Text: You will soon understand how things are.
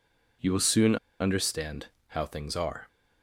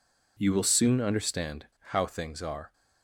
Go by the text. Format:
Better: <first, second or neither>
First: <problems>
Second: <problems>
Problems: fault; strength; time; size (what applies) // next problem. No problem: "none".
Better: second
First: pauses between "soon" and "understand"; slight; at 0.9 s; 0.24 s long // pauses between "understand" and "how"; slight; at 1.8 s; 0.22 s long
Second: pauses between "understand" and "how"; slight; at 1.6 s; 0.25 s long